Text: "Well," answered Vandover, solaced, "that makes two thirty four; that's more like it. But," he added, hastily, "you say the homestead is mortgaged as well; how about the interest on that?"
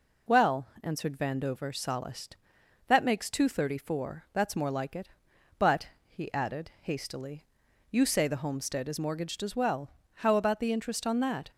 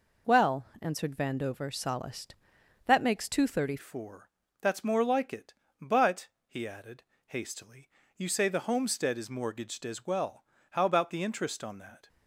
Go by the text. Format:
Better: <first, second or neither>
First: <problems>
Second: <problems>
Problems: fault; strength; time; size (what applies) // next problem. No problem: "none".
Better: first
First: none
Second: changes voice at "four"; from 3.7 s on; 8.3 s long